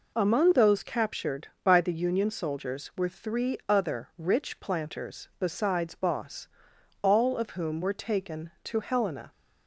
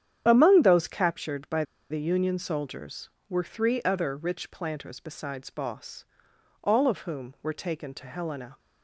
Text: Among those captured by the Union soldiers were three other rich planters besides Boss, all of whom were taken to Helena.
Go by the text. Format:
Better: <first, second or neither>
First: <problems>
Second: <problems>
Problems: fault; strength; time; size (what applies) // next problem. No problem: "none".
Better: first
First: none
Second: starts louder than the rest; strong; until 1.2 s; 9.5 dB // pauses between "by" and "the"; slight; at 1.6 s; 0.27 s long